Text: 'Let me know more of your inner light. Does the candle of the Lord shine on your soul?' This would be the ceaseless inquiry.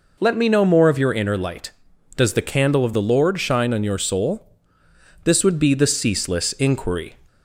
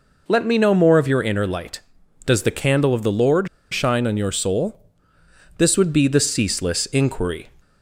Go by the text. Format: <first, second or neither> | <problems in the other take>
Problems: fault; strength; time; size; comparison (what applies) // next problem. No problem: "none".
first | pauses between "Lord" and "shine"; slight; at 3.4 s; 0.24 s long